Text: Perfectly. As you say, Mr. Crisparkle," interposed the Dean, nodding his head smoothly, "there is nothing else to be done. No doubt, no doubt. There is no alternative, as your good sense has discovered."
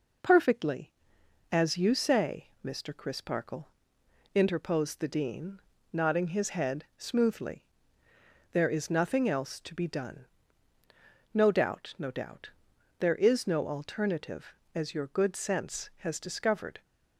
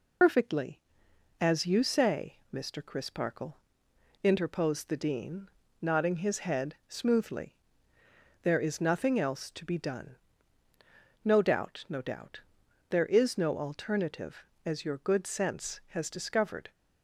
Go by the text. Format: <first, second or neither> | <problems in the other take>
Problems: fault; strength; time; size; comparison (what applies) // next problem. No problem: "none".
first | loses the start of "Perfectly"; at 0.2 s; 100 ms